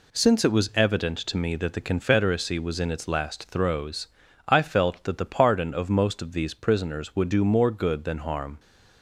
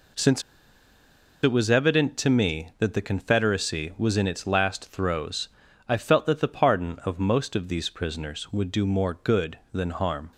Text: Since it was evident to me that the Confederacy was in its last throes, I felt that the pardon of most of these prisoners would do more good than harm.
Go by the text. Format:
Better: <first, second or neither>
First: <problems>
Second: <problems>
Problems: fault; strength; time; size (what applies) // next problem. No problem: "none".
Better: first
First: none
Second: pauses between "Since" and "it"; at 0.4 s; 1.0 s long